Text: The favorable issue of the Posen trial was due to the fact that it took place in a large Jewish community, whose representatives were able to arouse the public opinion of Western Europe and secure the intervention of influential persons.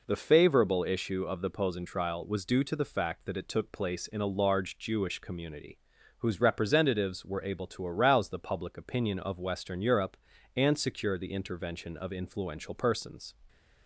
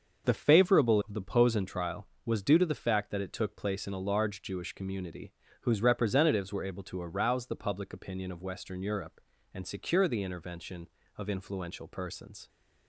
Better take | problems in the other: first | starts louder than the rest; until 1.3 s; 6.5 dB // skips "issue"; at 1.0 s

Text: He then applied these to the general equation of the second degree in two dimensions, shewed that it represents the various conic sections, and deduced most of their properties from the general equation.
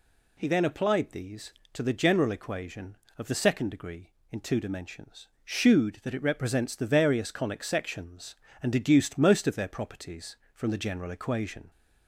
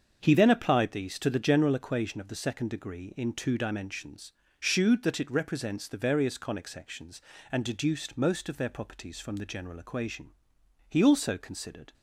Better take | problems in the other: first | starts louder than the rest; until 1.2 s; 7 dB // goes on to say "He also considered"; noticeable; from 10.8 s on; 1.0 s long

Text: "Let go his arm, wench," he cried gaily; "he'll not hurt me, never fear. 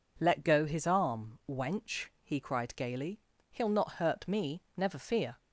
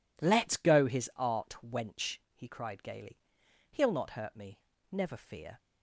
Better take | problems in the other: first | says "art" for "arm"; at 1.1 s

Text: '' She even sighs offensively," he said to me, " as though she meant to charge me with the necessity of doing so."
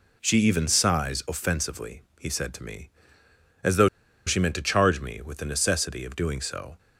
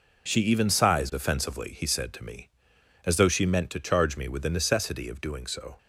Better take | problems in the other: second | pauses between "though" and "she"; at 3.8 s; 0.38 s long

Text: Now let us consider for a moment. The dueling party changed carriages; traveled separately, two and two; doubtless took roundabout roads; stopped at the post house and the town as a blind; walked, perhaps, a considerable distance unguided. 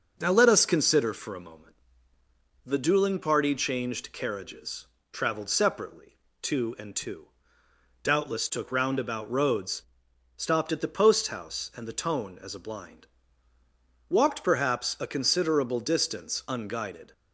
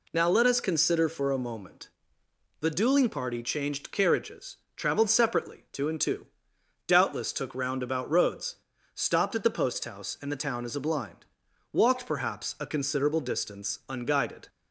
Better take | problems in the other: second | starts louder than the rest; until 1.2 s; 6.5 dB // says "tone" for "town"; at 11.9 s

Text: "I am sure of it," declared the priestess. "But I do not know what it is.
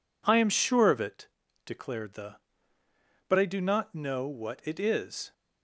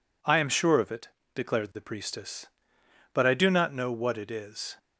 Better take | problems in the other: second | skips "priestess"; at 2.8 s

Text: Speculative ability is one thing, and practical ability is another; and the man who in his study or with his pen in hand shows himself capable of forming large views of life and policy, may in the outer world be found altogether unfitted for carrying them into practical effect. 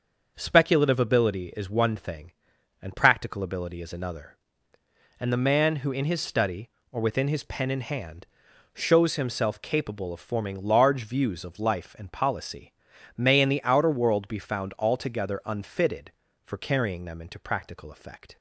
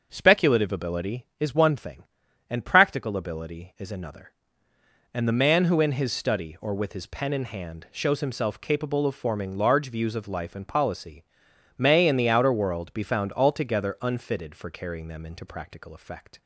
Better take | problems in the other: second | starts louder than the rest; until 1.3 s; 6 dB; also in the second // says "within" for "with"; at 6.9 s // pauses between "hand" and "shows"; noticeable; at 8.2 s; 0.48 s long

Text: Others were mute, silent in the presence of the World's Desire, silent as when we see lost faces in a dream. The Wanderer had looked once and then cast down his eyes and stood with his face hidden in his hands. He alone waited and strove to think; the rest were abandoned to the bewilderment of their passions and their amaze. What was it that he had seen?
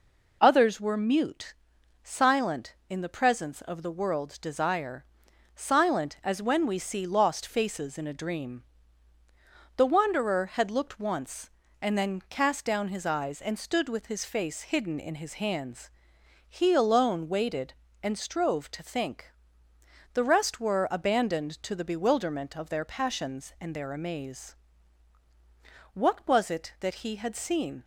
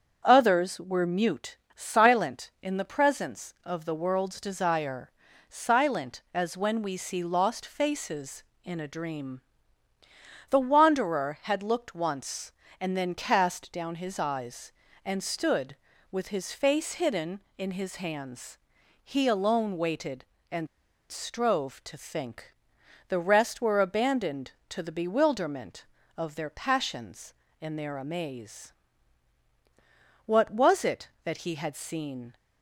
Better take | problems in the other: first | starts louder than the rest; strong; until 1.2 s; 7.5 dB // pauses between "and" and "strove"; at 20.6 s; 0.43 s long

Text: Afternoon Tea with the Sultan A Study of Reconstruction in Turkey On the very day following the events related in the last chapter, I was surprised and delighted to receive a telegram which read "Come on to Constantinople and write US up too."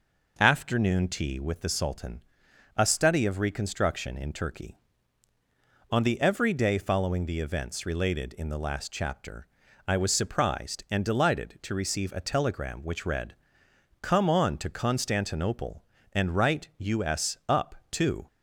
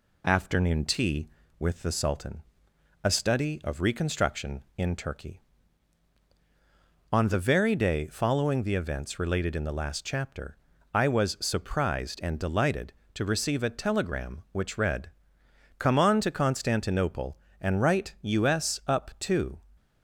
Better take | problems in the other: second | pauses between "Sultan" and "A"; noticeable; at 2.2 s; 0.56 s long; noticeable in the second // says "every" for "very"; at 6.2 s // pauses between "read" and "Come"; noticeable; at 13.3 s; 0.68 s long; noticeable in the second // pauses between "up" and "too"; slight; at 17.7 s; 0.16 s long

